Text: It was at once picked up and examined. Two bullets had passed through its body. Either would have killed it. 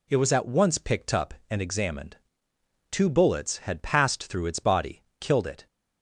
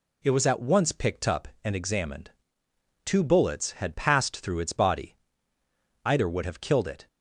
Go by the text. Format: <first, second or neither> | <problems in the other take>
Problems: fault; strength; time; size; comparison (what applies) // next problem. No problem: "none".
second | skips "Either would have"; at 5.1 s